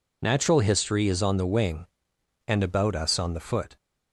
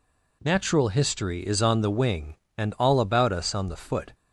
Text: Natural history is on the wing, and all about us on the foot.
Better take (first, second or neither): second